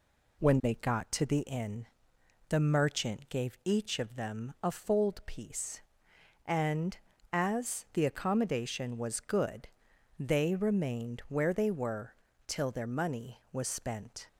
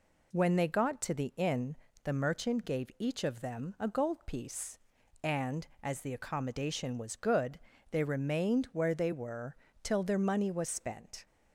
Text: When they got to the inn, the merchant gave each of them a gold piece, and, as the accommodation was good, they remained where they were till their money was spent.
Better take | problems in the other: second | says "fold" for "gold"; at 4.7 s // pauses between "were" and "till"; slight; at 12.1 s; 0.34 s long; slight in the second

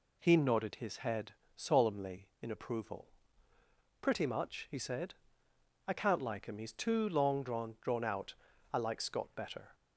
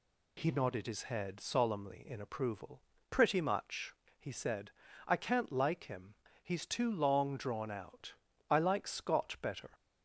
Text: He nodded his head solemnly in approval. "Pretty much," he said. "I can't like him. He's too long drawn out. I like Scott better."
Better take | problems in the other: second | pauses between "head" and "solemnly"; slight; at 1.3 s; 0.24 s long // says "drawn" twice; at 7.8 s

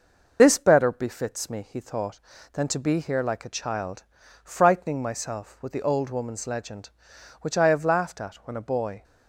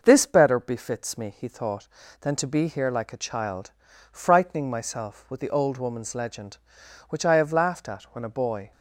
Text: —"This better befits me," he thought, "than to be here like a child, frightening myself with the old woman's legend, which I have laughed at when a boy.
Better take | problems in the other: second | loses the start of "This"; at 0.3 s; 45 ms

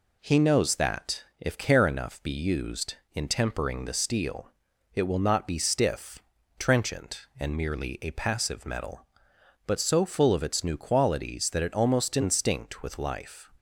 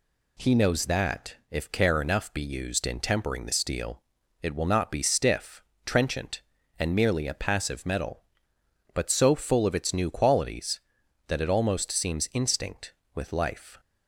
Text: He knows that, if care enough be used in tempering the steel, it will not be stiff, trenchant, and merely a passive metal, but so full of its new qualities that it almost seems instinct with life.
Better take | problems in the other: second | skips "seems"; at 12.1 s

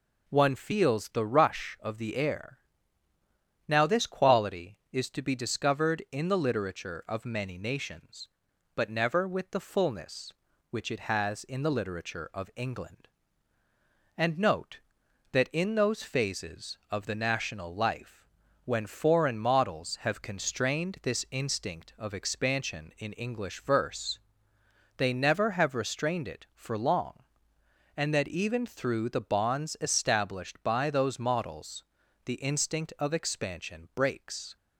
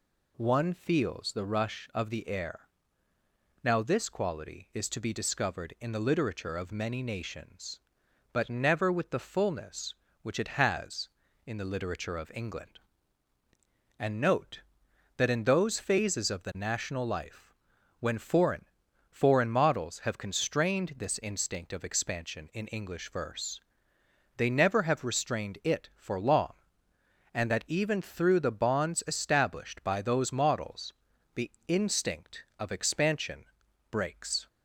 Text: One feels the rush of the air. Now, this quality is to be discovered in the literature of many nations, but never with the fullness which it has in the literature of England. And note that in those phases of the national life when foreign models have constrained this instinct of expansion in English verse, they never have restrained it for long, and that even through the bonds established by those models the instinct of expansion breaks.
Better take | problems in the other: first | pauses between "life" and "when"; at 17.5 s; 0.44 s long; also in the first // says "foreign" twice; at 19.0 s // pauses between "models" and "the"; at 30.9 s; 0.40 s long; also in the first // pauses between "the" and "instinct"; slight; at 31.4 s; 0.18 s long // pauses between "expansion" and "breaks"; at 33.4 s; 0.44 s long

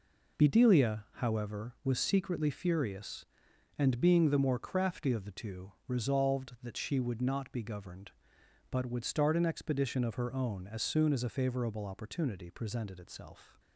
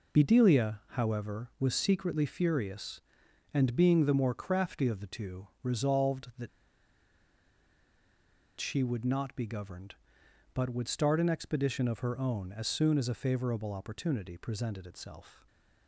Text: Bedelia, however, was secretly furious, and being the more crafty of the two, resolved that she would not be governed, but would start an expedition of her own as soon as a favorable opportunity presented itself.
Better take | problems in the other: first | pauses between "that" and "she"; strong; at 6.4 s; 2.1 s long // stays silent after the last word; slight; from 15.3 s on; 0.5 s long

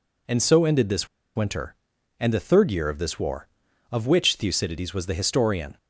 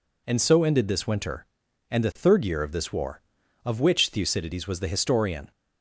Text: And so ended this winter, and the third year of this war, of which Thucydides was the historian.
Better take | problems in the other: second | pauses between "this" and "winter"; slight; at 1.0 s; 0.29 s long

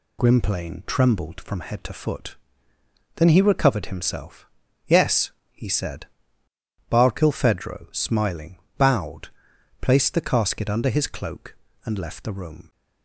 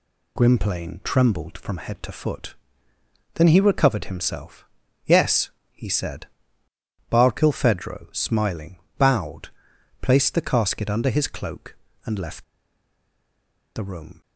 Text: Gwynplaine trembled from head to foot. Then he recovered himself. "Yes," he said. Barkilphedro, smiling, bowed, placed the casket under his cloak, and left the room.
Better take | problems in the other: first | pauses between "left" and "the"; strong; at 12.4 s; 1.3 s long

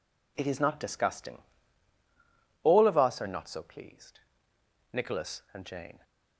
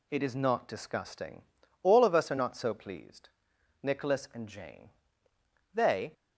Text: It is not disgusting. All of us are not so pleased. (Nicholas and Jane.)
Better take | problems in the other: first | goes on to say "They"; slight; from 5.7 s on; 0.40 s long

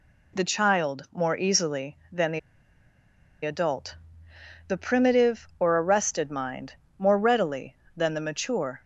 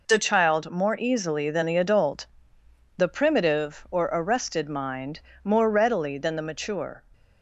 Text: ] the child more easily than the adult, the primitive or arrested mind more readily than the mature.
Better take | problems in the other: second | pauses between "the" and "adult"; at 2.3 s; 1.0 s long // pauses between "mind" and "more"; slight; at 6.7 s; 0.24 s long; slight in the second

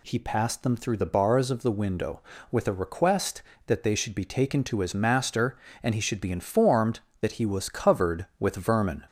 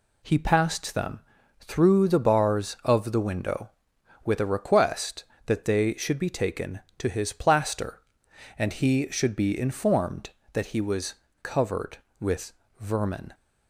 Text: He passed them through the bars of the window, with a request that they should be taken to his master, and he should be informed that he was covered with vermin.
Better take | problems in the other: first | pauses between "them" and "through"; at 1.1 s; 0.40 s long // says "plaster" for "master"; at 7.3 s // pauses between "was" and "covered"; slight; at 11.1 s; 0.27 s long // pauses between "with" and "vermin"; slight; at 12.5 s; 0.26 s long

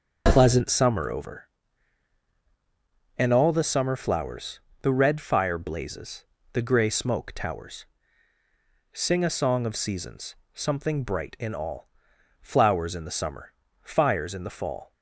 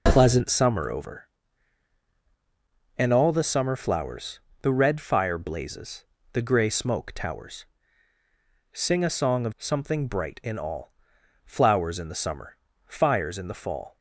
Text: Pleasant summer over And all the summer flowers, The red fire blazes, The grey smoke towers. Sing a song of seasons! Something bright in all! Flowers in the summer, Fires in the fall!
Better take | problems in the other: first | skips "seasons"; at 9.5 s

